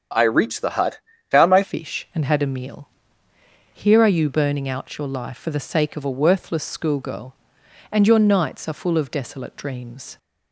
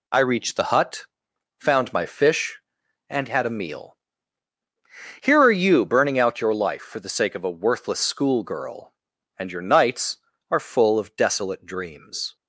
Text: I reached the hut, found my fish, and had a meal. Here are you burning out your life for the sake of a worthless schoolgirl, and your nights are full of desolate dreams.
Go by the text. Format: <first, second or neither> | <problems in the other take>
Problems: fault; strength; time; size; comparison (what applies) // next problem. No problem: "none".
second | starts louder than the rest; strong; until 1.4 s; 7 dB // changes voice at "fish"; from 1.6 s on; 8.5 s long